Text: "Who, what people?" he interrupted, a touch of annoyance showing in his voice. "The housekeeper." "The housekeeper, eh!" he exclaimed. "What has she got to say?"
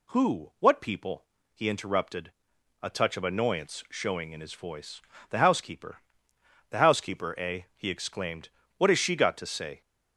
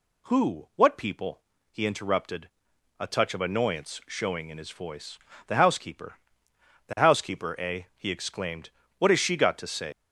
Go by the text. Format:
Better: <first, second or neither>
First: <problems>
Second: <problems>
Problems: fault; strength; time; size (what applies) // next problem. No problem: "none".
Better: first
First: none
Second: leaves "say" unfinished; at 9.9 s; 90 ms